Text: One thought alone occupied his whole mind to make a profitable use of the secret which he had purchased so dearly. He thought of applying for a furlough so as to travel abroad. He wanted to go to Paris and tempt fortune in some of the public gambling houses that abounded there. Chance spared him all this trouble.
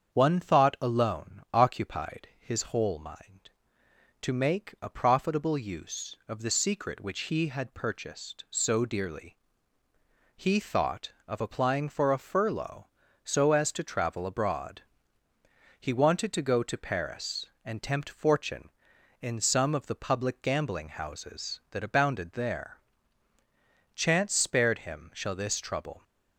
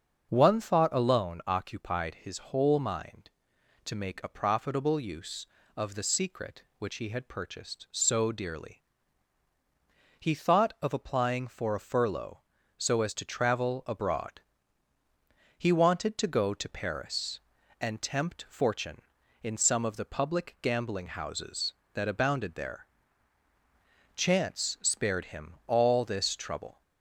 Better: second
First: starts louder than the rest; strong; until 1.1 s; 7.5 dB // says "shall" for "all"; at 25.1 s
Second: starts louder than the rest; until 1.3 s; 6.5 dB

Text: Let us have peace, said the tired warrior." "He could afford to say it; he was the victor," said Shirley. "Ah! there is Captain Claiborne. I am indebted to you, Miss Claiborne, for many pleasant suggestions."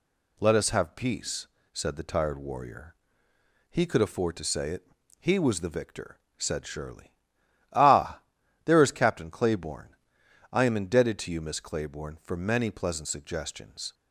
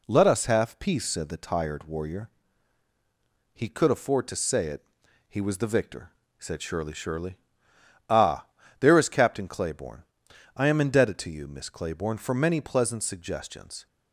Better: first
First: none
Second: says "Shirley" twice; at 6.9 s

